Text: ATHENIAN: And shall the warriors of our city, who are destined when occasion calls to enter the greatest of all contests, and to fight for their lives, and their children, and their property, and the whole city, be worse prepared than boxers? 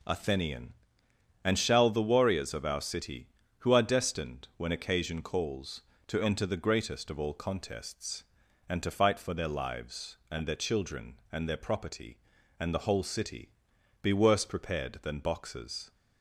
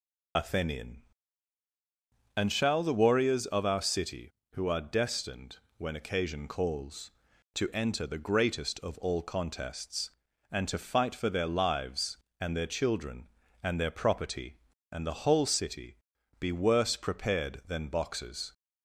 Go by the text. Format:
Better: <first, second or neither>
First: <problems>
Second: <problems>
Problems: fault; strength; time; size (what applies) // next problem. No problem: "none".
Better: first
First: none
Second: loses the start of "ATHENIAN"; at 0.3 s; 60 ms // pauses between "destined" and "when"; slight; at 5.5 s; 0.22 s long